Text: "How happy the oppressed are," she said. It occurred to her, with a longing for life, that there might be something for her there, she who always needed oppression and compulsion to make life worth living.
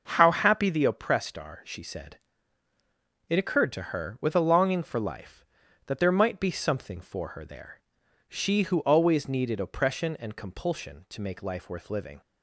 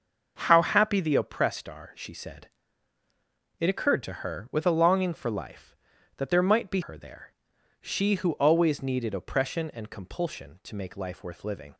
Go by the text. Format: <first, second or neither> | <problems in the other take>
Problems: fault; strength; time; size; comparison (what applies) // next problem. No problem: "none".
first | starts louder than the rest; until 1.4 s; 6 dB; noticeable in the first // skips "something for"; at 6.8 s